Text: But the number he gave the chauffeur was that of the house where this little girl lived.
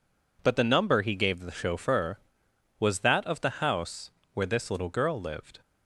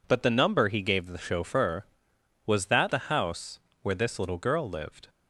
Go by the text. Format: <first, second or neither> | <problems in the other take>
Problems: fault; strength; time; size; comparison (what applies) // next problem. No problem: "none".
first | skips "of"; at 2.9 s // pauses between "house" and "where"; slight; at 3.5 s; 0.24 s long; slight in the first